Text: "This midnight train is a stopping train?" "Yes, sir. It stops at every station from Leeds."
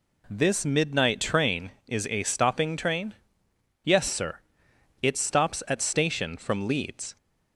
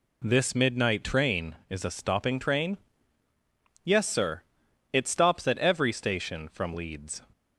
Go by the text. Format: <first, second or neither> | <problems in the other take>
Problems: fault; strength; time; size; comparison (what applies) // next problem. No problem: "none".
second | skips "every"; at 5.8 s